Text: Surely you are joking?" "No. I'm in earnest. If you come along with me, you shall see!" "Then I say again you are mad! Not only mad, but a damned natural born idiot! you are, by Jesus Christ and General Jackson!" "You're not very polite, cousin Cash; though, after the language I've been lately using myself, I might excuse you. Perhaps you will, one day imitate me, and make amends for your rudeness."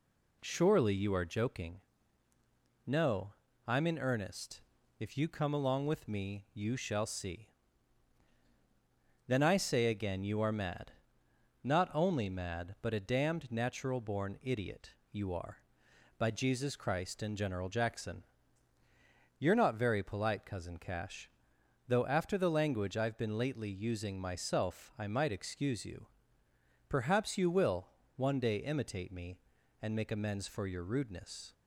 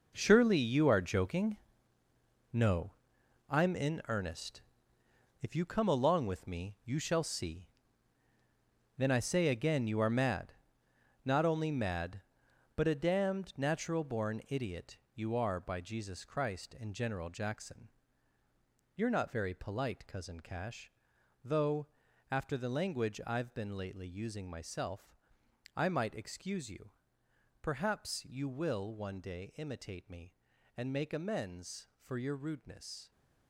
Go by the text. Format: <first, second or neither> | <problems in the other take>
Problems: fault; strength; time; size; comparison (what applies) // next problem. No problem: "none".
first | gets quieter; strong; throughout; 11.5 dB